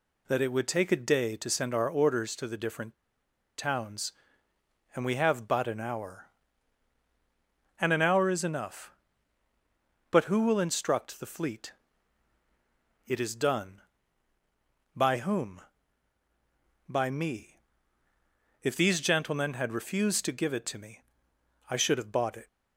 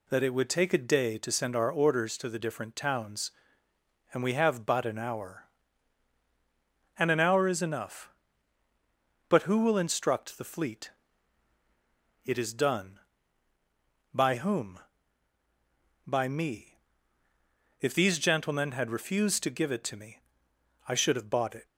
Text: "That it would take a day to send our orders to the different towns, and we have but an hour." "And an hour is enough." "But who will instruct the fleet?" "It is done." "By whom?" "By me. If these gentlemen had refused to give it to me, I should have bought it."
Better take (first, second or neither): second